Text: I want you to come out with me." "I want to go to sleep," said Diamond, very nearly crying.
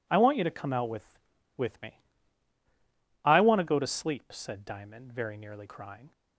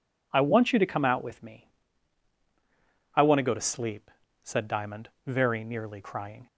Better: second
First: says "with" twice; at 1.5 s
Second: none

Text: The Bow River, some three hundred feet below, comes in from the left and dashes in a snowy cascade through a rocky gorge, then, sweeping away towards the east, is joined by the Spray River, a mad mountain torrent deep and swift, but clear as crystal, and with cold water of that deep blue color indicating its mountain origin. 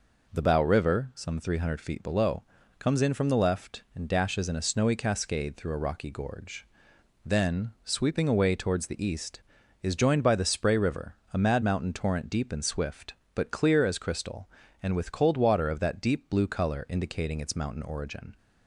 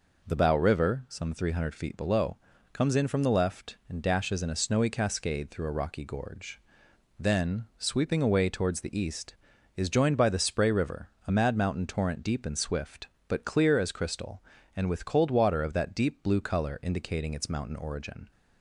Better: neither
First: none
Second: none

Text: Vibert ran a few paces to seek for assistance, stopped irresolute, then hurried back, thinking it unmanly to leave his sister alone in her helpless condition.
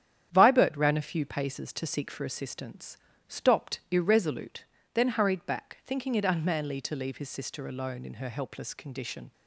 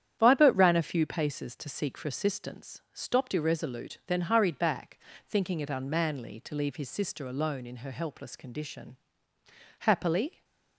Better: first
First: starts louder than the rest; strong; until 1.3 s; 9.5 dB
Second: starts louder than the rest; strong; until 1.2 s; 9.5 dB // goes on to say "Happily"; noticeable; from 9.7 s on; 0.64 s long

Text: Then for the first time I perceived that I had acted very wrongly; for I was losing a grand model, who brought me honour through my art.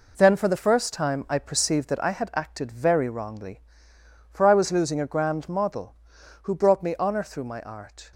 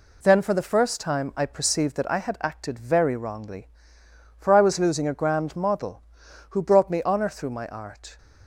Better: second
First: gets quieter; strong; throughout; 7.5 dB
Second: none

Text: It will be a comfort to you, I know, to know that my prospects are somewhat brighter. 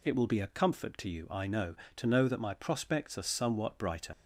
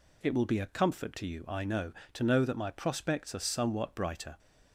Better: second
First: leaves "brighter" unfinished; at 4.1 s; 85 ms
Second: none

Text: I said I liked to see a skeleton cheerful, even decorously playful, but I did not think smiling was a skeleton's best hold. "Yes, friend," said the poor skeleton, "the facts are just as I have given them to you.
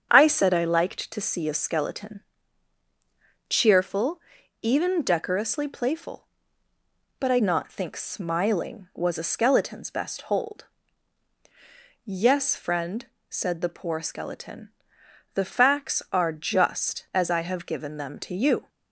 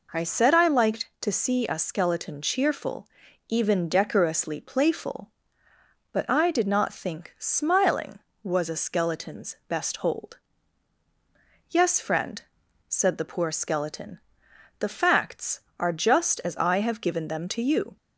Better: second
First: starts louder than the rest; strong; until 1.1 s; 8 dB // pauses between "skeleton" and "cheerful"; strong; at 2.2 s; 1.2 s long // skips "did"; at 7.3 s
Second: none

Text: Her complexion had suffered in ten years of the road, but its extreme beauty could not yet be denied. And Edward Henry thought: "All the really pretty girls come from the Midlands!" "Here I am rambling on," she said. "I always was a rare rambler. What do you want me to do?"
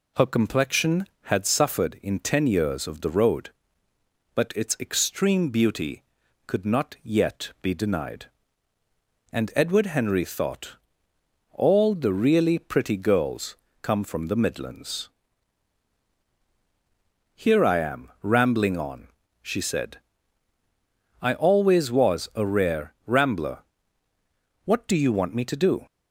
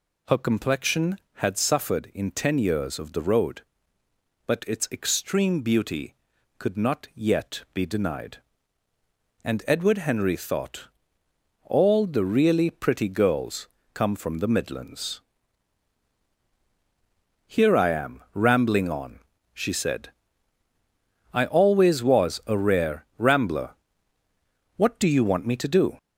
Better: first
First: pauses between "girls" and "come"; slight; at 13.5 s; 0.26 s long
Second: gets louder; noticeable; throughout; 4.5 dB // pauses between "girls" and "come"; slight; at 13.6 s; 0.26 s long

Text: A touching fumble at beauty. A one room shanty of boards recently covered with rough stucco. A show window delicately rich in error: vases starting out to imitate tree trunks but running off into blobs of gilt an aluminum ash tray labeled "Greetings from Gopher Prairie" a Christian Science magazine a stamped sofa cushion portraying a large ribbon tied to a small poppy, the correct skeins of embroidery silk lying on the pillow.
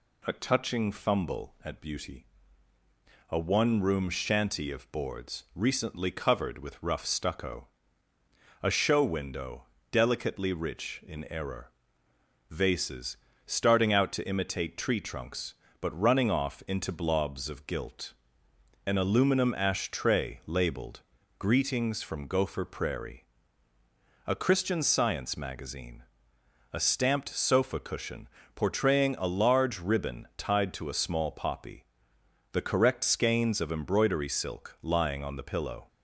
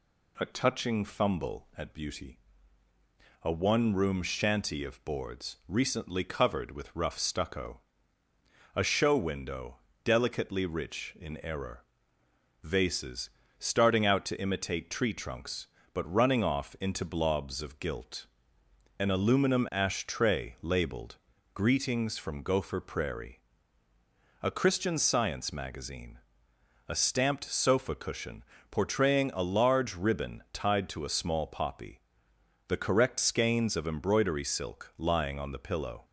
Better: neither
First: pauses between "window" and "delicately"; slight; at 9.6 s; 0.28 s long // pauses between "vases" and "starting"; slight; at 13.1 s; 0.28 s long // pauses between "gilt" and "an"; noticeable; at 18.1 s; 0.72 s long // pauses between "labeled" and "Greetings"; slight; at 21.0 s; 0.36 s long // pauses between "Prairie" and "a"; at 23.2 s; 1.0 s long // pauses between "magazine" and "a"; noticeable; at 26.0 s; 0.72 s long // pauses between "cushion" and "portraying"; slight; at 28.2 s; 0.28 s long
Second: pauses between "window" and "delicately"; slight; at 9.7 s; 0.28 s long // pauses between "vases" and "starting"; slight; at 13.3 s; 0.28 s long // pauses between "gilt" and "an"; noticeable; at 18.2 s; 0.72 s long // pauses between "labeled" and "Greetings"; slight; at 21.1 s; 0.36 s long // pauses between "Prairie" and "a"; at 23.4 s; 1.0 s long // pauses between "magazine" and "a"; noticeable; at 26.1 s; 0.72 s long // pauses between "cushion" and "portraying"; slight; at 28.4 s; 0.28 s long

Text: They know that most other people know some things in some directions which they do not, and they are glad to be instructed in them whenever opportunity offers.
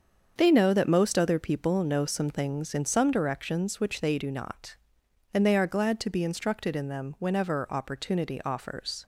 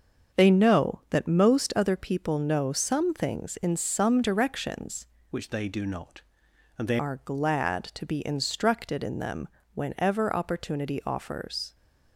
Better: first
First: starts louder than the rest; until 1.3 s; 7 dB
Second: starts louder than the rest; until 1.4 s; 6.5 dB // changes voice from "which" to "they"; from 5.3 to 6.9 s; 1.6 s long // pauses between "them" and "whenever"; slight; at 9.4 s; 0.28 s long

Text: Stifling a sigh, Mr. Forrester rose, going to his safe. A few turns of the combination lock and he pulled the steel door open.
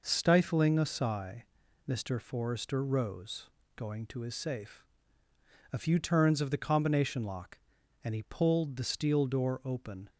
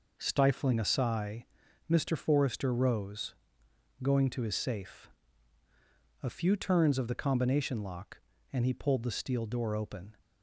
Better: neither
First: none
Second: none

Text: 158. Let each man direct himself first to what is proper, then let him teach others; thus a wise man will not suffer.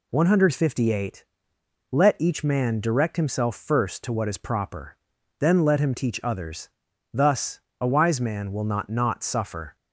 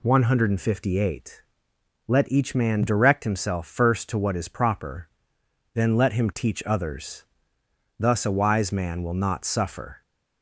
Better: second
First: pauses between "thus" and "a"; slight; at 7.5 s; 0.22 s long // says "not" twice; at 8.8 s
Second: none

